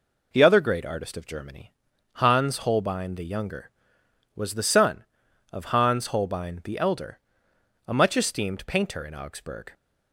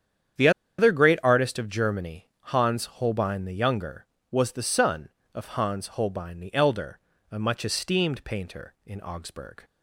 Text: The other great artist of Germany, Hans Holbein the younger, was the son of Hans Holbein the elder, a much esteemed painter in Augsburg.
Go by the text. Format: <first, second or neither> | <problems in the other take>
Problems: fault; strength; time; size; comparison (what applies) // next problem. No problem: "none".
first | starts louder than the rest; strong; until 1.7 s; 8.5 dB // pauses between "The" and "other"; slight; at 0.4 s; 0.28 s long